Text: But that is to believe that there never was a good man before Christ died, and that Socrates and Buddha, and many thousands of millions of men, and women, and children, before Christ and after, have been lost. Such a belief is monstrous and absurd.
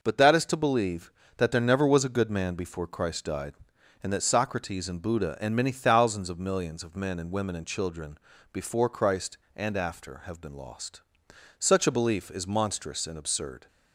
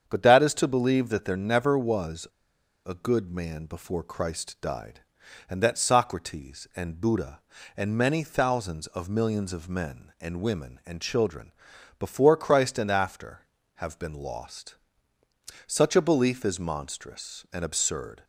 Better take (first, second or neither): first